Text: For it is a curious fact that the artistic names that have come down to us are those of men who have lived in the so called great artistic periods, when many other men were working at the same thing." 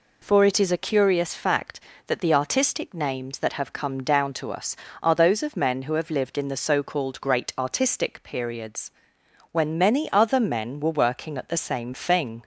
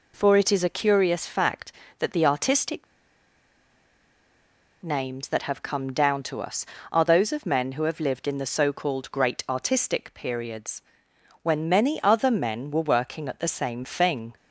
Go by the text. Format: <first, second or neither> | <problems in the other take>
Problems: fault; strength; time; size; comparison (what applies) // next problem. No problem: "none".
first | pauses between "artistic" and "names"; strong; at 2.8 s; 1.9 s long